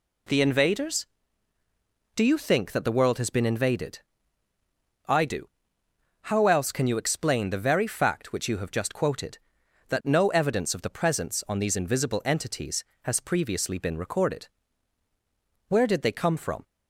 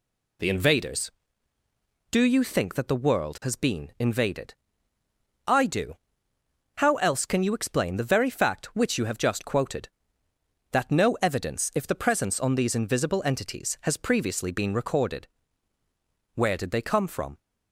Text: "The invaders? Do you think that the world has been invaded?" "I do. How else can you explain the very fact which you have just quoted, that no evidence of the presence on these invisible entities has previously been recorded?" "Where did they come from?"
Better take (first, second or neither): first